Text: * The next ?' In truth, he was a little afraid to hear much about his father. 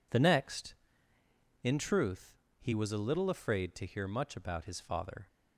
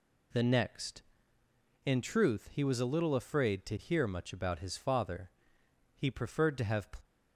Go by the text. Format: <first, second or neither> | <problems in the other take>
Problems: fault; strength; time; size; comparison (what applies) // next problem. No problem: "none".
first | goes on to say "He preferred to have"; noticeable; from 5.9 s on; 0.92 s long